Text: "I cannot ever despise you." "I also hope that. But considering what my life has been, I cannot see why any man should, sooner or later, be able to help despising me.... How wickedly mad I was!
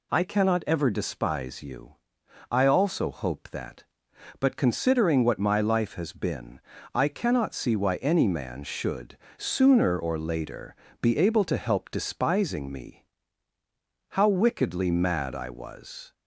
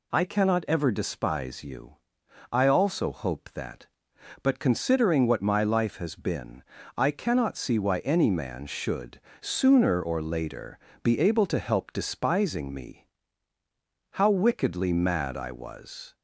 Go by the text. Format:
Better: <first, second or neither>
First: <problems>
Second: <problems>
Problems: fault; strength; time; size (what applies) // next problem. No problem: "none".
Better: neither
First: none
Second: none